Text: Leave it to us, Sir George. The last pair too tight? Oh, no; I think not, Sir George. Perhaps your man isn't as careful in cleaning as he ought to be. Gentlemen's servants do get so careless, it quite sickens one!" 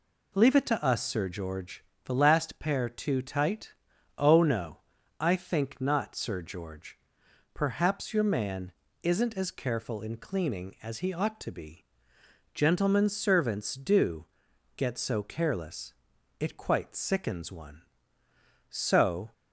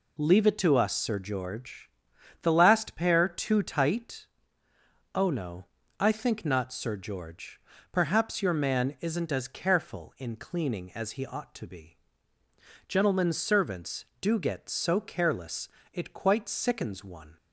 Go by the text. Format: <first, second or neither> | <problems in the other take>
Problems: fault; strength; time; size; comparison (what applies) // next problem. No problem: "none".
second | pauses between "man" and "isn't"; slight; at 8.7 s; 0.30 s long // pauses between "do" and "get"; noticeable; at 14.2 s; 0.52 s long // goes on to say "So"; noticeable; from 18.7 s on; 0.62 s long